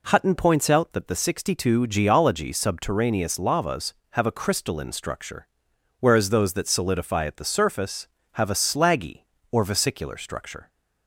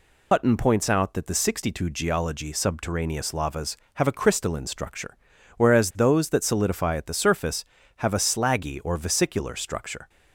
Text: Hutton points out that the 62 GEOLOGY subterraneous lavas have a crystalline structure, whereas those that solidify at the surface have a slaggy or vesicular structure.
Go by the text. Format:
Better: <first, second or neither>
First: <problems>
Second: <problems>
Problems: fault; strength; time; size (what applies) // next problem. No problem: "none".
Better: first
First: none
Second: loses the start of "Hutton"; at 0.3 s; 95 ms